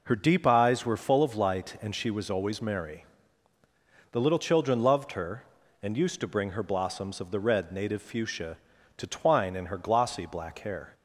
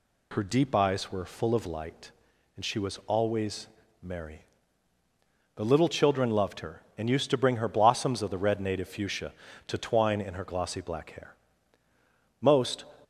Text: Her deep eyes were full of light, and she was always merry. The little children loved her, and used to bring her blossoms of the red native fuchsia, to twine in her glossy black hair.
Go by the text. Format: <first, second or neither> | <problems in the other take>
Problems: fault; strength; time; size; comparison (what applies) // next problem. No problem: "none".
first | pauses between "always" and "merry"; slight; at 3.6 s; 0.36 s long // goes on to say "Most"; slight; from 12.4 s on; 0.46 s long